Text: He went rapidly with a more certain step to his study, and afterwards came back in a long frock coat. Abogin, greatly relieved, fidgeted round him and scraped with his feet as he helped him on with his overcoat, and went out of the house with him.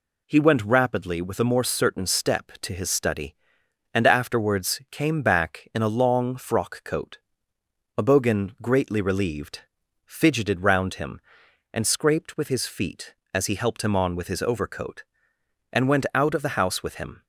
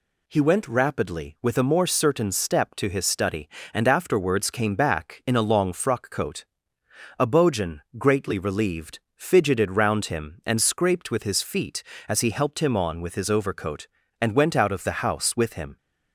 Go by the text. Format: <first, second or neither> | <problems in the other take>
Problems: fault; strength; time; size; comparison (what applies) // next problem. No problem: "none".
neither | none